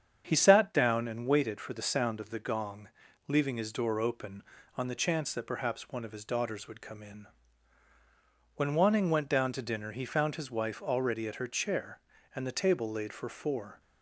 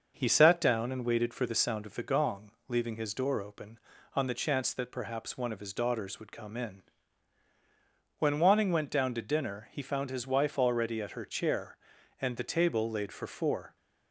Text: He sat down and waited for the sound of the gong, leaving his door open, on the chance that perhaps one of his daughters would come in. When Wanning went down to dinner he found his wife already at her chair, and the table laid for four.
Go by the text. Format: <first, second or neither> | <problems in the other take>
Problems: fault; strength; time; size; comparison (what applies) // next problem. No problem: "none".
neither | starts louder than the rest; the same in both